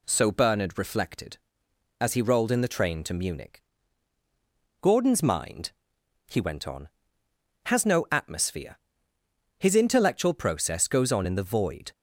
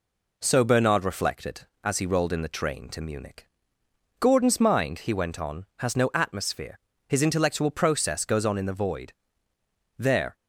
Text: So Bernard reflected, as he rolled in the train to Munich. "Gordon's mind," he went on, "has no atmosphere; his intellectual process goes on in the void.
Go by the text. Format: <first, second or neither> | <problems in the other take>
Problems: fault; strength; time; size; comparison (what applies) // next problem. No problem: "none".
first | goes on to say "There"; slight; from 9.9 s on; 0.38 s long